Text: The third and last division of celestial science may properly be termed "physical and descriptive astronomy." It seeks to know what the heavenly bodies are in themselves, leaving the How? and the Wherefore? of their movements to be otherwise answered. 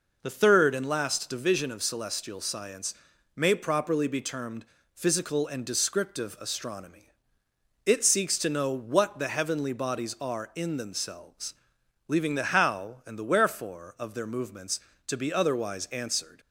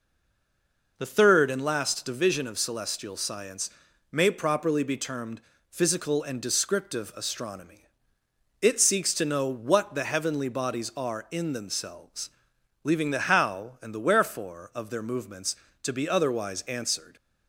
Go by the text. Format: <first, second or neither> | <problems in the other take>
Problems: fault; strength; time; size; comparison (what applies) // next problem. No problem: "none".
first | stays silent before the first word; until 0.9 s; 0.9 s long // pauses between "science" and "may"; at 3.6 s; 0.42 s long; also in the first // pauses between "termed" and "physical"; slight; at 5.4 s; 0.28 s long; slight in the first